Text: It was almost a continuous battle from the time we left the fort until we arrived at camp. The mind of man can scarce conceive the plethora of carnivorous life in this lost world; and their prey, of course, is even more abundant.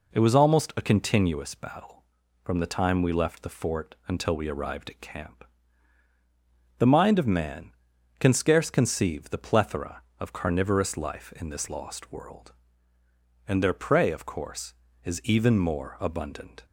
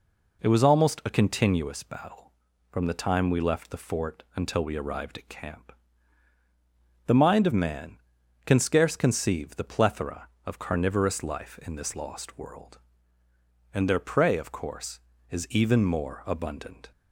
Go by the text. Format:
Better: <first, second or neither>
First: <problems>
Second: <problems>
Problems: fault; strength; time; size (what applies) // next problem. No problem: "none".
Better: neither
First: none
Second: none